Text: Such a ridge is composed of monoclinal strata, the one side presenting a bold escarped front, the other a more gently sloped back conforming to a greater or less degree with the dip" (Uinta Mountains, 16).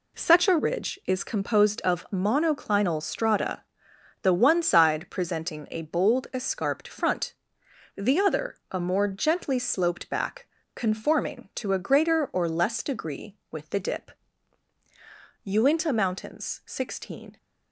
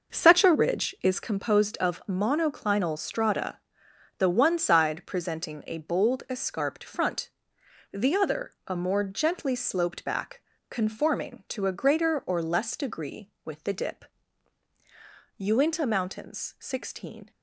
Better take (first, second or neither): first